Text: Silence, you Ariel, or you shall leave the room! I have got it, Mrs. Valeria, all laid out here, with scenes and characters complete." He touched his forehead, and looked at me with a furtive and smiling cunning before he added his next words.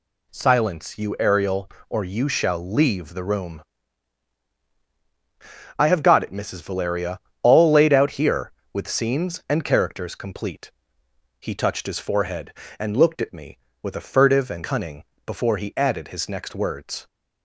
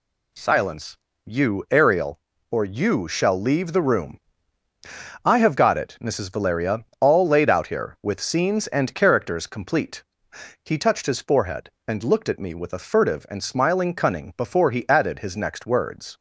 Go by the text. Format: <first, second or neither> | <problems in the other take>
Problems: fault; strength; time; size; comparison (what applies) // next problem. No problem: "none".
second | skips "smiling"; at 14.6 s // pauses between "cunning" and "before"; slight; at 15.0 s; 0.22 s long